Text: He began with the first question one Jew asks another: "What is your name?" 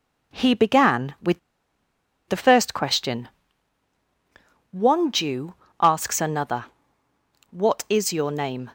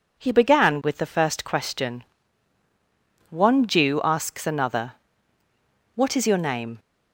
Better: second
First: pauses between "with" and "the"; noticeable; at 1.3 s; 0.90 s long // pauses between "question" and "one"; strong; at 3.2 s; 1.4 s long // pauses between "Jew" and "asks"; slight; at 5.5 s; 0.24 s long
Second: pauses between "question" and "one"; strong; at 2.0 s; 1.2 s long

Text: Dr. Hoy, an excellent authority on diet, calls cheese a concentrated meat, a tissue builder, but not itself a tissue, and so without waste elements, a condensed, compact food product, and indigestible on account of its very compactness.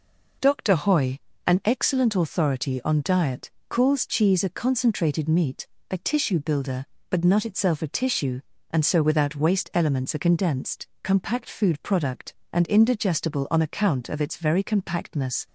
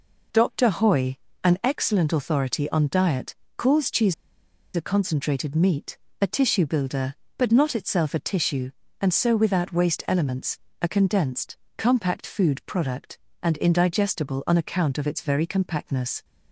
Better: first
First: none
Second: pauses between "cheese" and "a"; noticeable; at 4.1 s; 0.60 s long

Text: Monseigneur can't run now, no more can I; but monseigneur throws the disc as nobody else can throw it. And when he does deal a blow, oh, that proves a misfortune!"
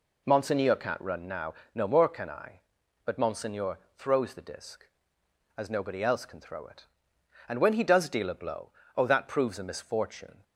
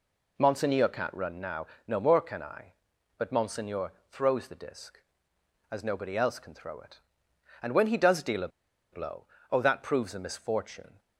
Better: first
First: pauses between "monseigneur" and "throws"; slight; at 3.7 s; 0.18 s long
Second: pauses between "monseigneur" and "throws"; slight; at 3.9 s; 0.18 s long // pauses between "a" and "blow"; at 8.4 s; 0.44 s long

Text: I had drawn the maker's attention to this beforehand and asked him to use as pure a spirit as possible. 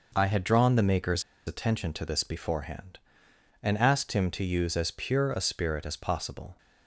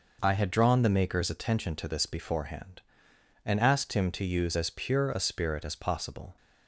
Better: second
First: pauses between "maker's" and "attention"; slight; at 1.2 s; 0.24 s long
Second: none

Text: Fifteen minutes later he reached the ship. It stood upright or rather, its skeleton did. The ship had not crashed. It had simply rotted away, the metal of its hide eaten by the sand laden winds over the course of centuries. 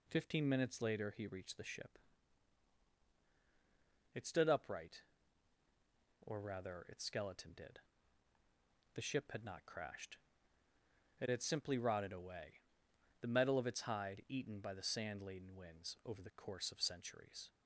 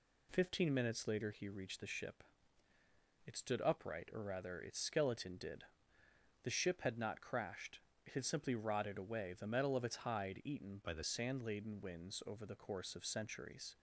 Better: first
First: none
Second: changes voice from "by" to "the"; from 10.8 to 11.0 s; 0.2 s long

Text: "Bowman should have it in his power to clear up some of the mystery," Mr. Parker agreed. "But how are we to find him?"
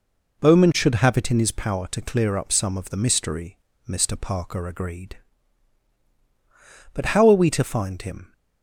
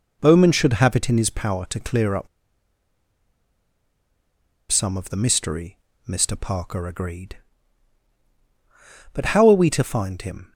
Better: first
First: none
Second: pauses between "up" and "some"; strong; at 2.2 s; 2.4 s long

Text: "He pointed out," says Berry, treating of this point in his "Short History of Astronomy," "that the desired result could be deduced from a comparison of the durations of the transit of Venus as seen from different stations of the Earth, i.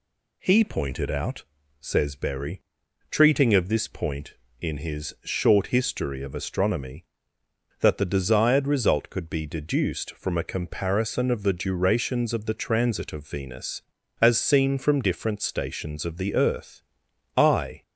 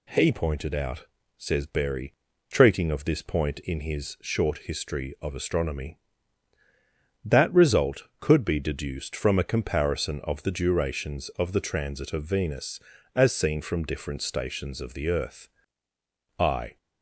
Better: first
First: none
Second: skips "the desired"; at 7.5 s

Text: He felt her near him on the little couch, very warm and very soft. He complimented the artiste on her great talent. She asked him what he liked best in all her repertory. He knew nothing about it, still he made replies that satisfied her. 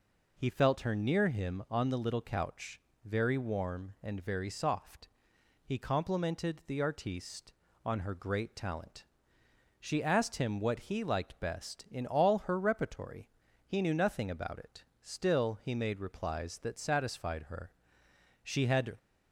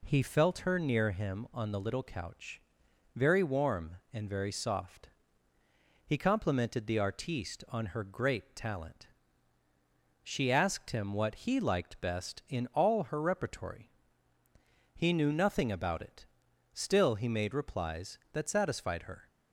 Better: second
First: goes on to say "She had"; from 18.4 s on; 0.52 s long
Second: none

